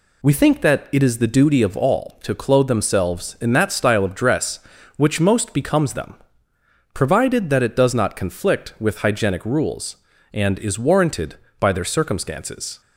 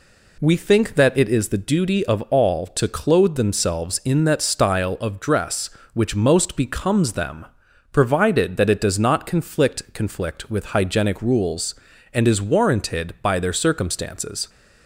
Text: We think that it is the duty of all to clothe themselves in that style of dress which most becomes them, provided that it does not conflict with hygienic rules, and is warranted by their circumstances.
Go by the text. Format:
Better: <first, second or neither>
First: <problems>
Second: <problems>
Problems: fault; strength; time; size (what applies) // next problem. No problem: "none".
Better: first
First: none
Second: says "conflict" twice; at 9.9 s